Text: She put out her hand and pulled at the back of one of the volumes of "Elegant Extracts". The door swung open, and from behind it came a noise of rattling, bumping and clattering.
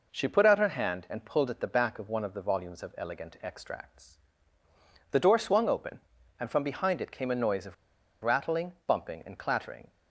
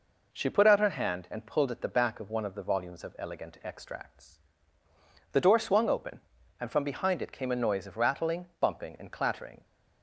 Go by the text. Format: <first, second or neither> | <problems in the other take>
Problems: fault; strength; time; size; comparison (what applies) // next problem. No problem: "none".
second | pauses between "of" and "rattling"; noticeable; at 7.7 s; 0.49 s long